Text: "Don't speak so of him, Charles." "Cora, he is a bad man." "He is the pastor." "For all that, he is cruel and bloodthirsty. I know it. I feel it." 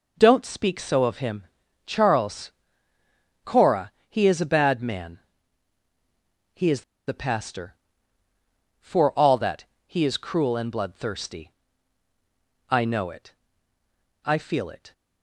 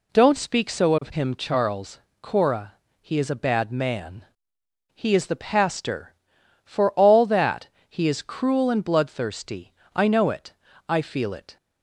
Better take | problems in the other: second | pauses between "is" and "the"; slight; at 6.8 s; 0.26 s long

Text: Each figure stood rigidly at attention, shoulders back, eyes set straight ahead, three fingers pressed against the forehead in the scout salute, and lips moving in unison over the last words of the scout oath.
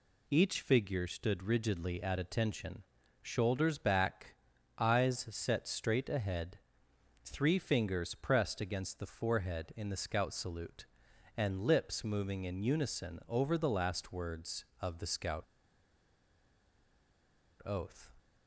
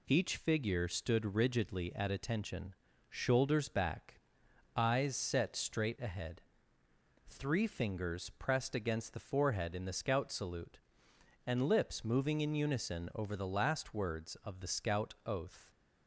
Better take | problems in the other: second | pauses between "scout" and "oath"; strong; at 15.4 s; 2.1 s long

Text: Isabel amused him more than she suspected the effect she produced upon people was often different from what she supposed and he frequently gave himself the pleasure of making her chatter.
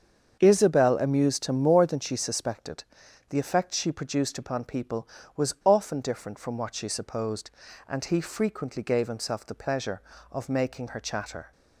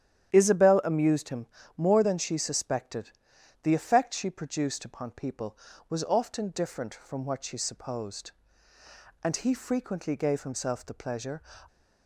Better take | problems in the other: first | starts louder than the rest; strong; until 1.3 s; 10 dB; strong in the first // pauses between "him" and "more"; slight; at 1.4 s; 0.30 s long // pauses between "suspected" and "the"; noticeable; at 3.1 s; 0.50 s long; noticeable in the first // stops before "of making her chatter"; at 11.6 s

